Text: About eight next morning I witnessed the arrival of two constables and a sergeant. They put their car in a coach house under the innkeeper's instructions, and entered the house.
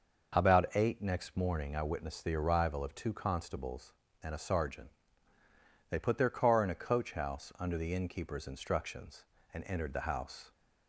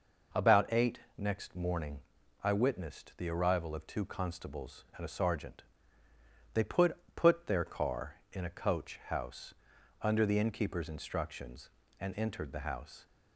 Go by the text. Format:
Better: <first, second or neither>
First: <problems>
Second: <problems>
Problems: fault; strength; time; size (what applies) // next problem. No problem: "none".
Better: first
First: none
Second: pauses between "eight" and "next"; slight; at 0.9 s; 0.18 s long // pauses between "morning" and "I"; at 1.9 s; 0.42 s long // says "put" twice; at 7.1 s // pauses between "house" and "under"; noticeable; at 9.5 s; 0.48 s long